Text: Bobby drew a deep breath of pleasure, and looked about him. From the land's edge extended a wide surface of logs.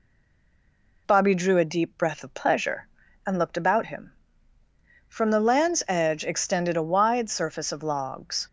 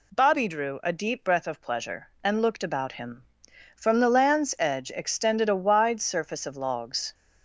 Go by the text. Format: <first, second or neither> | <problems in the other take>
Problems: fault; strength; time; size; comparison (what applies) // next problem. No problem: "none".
second | stays silent before the first word; slight; until 1.0 s; 1.0 s long